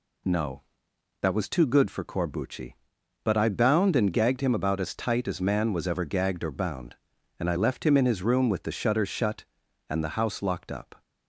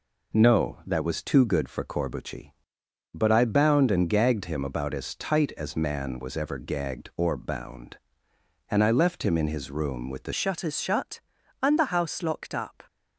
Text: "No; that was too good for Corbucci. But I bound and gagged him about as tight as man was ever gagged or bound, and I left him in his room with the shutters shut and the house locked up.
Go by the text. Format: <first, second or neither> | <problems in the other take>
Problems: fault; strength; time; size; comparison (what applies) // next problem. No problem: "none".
first | changes voice at "shutters"; from 10.3 s on; 2.5 s long